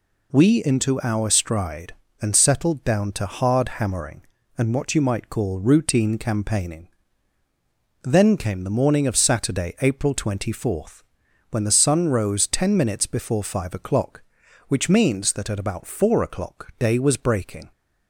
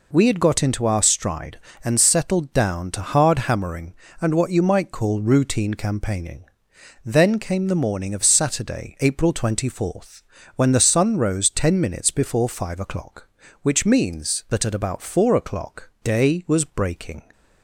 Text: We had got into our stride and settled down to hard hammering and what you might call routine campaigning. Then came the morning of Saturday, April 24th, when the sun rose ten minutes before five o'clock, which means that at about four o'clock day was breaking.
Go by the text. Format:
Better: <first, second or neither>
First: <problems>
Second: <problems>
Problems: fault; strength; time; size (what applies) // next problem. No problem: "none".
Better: second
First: skips "had got"; at 0.6 s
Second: none